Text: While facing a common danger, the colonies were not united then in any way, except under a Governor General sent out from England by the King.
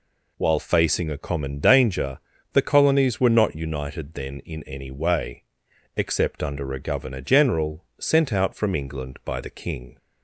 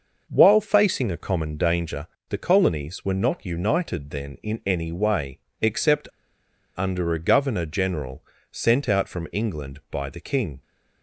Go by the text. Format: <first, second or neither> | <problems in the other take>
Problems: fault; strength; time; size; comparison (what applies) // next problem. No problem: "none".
first | pauses between "except" and "under"; noticeable; at 6.0 s; 0.66 s long // pauses between "General" and "sent"; slight; at 8.2 s; 0.30 s long